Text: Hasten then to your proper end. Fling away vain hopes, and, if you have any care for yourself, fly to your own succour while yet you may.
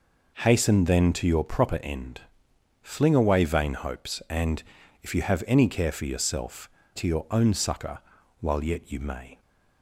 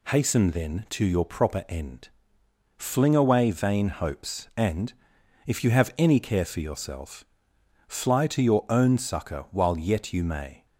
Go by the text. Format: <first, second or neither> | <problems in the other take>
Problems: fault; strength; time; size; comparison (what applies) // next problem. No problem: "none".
second | skips "fly"; at 6.8 s // pauses between "succour" and "while"; at 7.9 s; 0.40 s long